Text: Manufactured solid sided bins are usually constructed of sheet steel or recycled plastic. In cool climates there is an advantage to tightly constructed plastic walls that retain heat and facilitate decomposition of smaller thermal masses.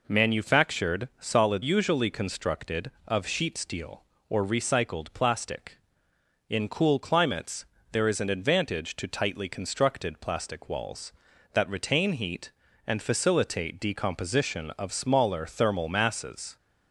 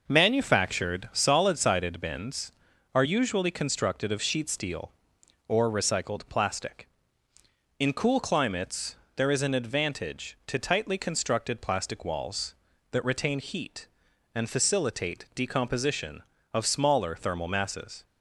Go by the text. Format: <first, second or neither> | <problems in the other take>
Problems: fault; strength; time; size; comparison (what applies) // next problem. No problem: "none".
second | skips "sided bins are"; at 1.6 s // pauses between "climates" and "there"; slight; at 7.6 s; 0.28 s long; slight in the second